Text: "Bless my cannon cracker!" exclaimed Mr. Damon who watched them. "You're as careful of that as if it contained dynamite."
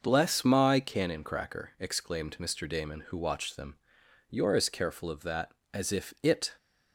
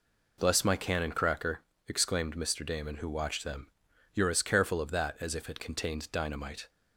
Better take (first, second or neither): second